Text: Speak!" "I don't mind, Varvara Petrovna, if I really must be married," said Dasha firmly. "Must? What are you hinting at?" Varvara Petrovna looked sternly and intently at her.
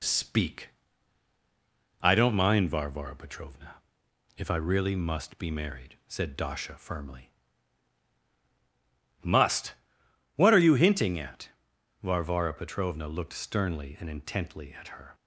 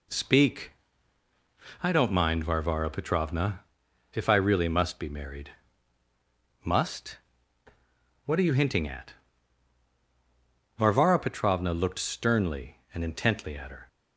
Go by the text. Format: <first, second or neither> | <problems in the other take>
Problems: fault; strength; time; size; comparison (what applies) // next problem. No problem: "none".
first | skips "said Dasha firmly"; at 6.0 s